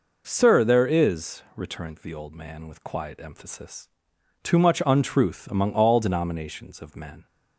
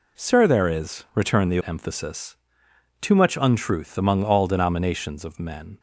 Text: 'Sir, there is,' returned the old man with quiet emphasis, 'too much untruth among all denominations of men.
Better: first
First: none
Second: skips "old man with quiet"; at 1.6 s

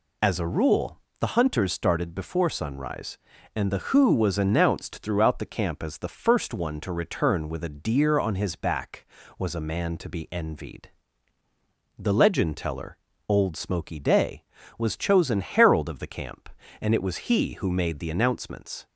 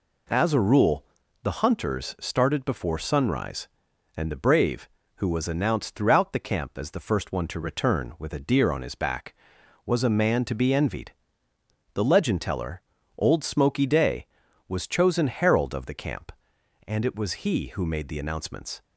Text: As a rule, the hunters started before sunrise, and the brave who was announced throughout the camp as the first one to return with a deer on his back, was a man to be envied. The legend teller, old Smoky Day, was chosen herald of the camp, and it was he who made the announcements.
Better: second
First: skips "brave"; at 3.9 s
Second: none

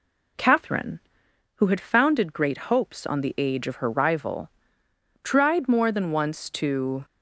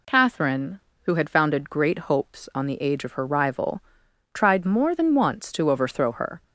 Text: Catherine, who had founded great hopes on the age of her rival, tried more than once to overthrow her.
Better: second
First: stops before "overthrow her"; at 7.0 s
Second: none

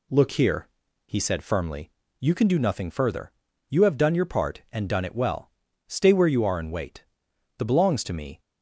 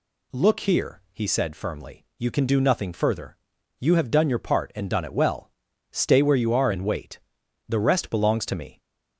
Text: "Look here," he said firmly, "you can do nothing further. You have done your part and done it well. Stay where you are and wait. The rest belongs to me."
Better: second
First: skips "rest"; at 7.6 s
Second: none

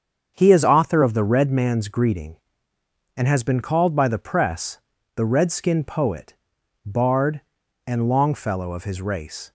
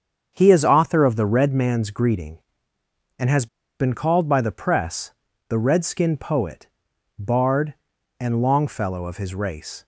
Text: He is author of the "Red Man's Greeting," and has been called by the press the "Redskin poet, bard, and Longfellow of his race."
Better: first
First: starts louder than the rest; strong; until 1.3 s; 7 dB // pauses between "press" and "the"; slight; at 4.7 s; 0.36 s long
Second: starts louder than the rest; strong; until 1.3 s; 7 dB // pauses between "has" and "been"; slight; at 3.4 s; 0.33 s long // pauses between "press" and "the"; slight; at 5.1 s; 0.36 s long

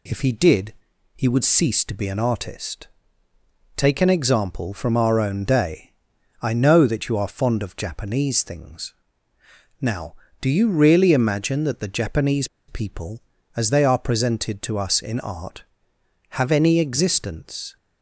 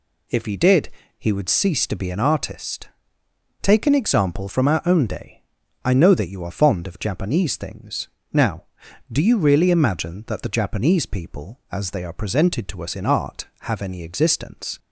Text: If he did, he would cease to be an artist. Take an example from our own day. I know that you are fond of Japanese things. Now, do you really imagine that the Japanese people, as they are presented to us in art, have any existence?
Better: second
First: pauses between "Japanese" and "people"; slight; at 12.4 s; 0.21 s long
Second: none

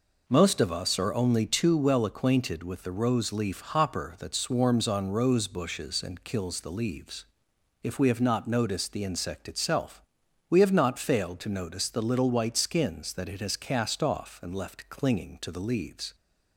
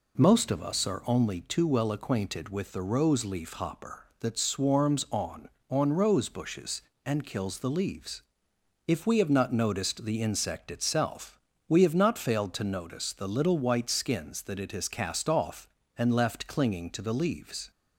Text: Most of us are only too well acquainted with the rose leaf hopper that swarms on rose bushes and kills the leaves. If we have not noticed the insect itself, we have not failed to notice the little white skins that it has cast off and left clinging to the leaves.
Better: first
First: none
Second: says "on" twice; at 5.6 s

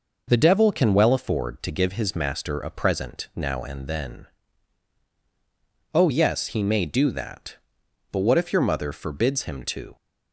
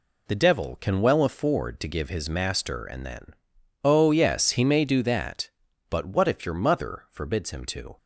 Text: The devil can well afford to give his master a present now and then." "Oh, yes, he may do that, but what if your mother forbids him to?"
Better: first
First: none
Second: skips "a present now"; at 2.8 s

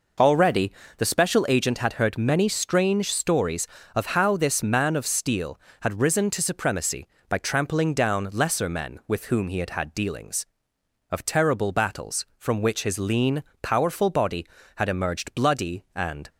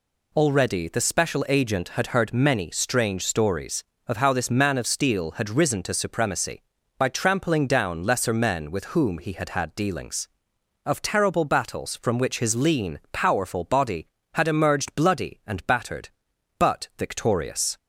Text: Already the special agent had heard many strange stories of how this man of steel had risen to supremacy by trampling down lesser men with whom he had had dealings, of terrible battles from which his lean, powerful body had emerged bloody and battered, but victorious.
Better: second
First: pauses between "Already" and "the"; slight; at 0.7 s; 0.24 s long // stops before "battered but victorious"; at 16.2 s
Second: none

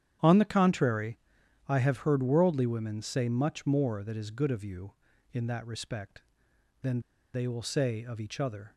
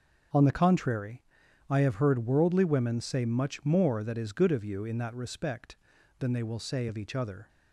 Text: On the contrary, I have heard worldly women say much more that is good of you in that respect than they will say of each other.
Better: second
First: starts louder than the rest; strong; until 1.7 s; 9.5 dB // pauses between "than" and "they"; slight; at 6.9 s; 0.34 s long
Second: starts louder than the rest; until 1.8 s; 6.5 dB

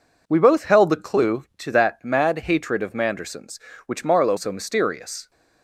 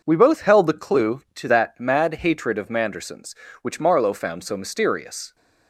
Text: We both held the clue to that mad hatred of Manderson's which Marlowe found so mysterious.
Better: second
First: skips "found"; at 4.3 s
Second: none

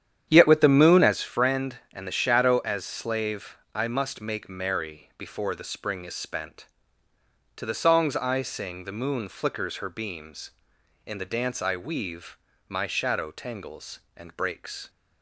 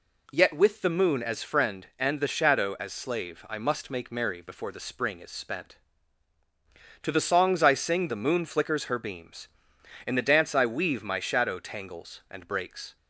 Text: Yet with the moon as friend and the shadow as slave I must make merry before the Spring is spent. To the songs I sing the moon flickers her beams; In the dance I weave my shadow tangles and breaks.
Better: second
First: starts louder than the rest; strong; until 1.2 s; 9.5 dB // pauses between "slave" and "I"; slight; at 3.5 s; 0.18 s long // pauses between "weave" and "my"; slight; at 12.3 s; 0.32 s long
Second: none

